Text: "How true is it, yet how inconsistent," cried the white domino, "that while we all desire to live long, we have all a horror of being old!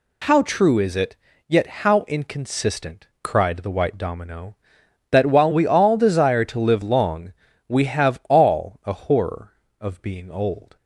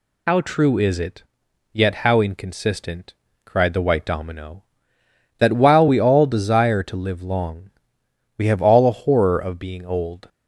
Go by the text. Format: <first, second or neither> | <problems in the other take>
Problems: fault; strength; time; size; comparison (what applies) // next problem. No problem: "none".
first | loses the start of "How"; at 0.2 s; 70 ms